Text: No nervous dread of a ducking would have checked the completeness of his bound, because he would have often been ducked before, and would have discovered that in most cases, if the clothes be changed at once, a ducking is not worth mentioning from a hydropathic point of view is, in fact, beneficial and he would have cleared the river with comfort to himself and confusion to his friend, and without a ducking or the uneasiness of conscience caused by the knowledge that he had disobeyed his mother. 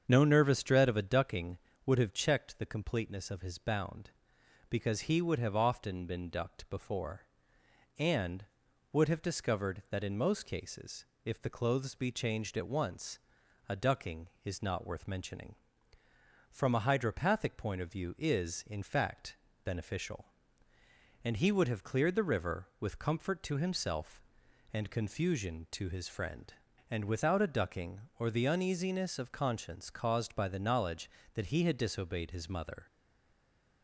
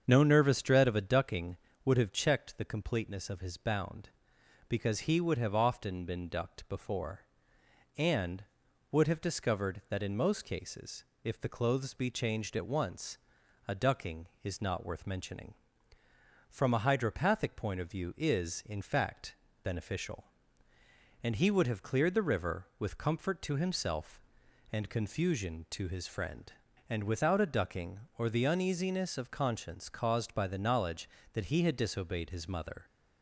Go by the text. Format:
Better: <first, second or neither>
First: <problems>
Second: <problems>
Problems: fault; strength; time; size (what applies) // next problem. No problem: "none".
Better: second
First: starts louder than the rest; strong; until 1.0 s; 7 dB // stays silent after the last word; from 32.8 s on; 1.0 s long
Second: starts louder than the rest; strong; until 1.0 s; 7 dB